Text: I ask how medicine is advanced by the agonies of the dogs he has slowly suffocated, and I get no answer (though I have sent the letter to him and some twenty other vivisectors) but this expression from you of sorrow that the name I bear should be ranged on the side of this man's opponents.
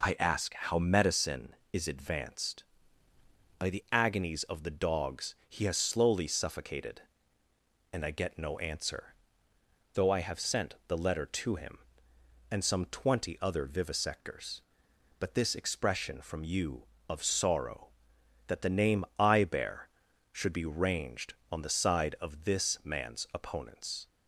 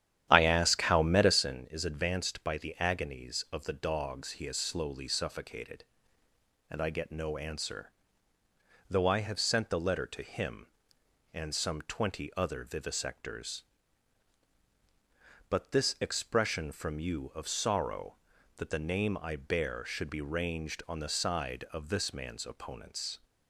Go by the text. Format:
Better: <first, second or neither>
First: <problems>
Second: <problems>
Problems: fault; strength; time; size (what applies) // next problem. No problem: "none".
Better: first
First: none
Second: starts louder than the rest; strong; until 1.5 s; 10.5 dB